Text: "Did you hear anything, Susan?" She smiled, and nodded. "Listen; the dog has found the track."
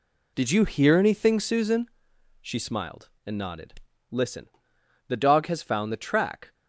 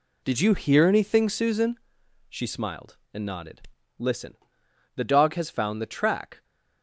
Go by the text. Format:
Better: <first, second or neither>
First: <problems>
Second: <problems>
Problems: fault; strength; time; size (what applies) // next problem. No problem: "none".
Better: neither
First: none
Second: none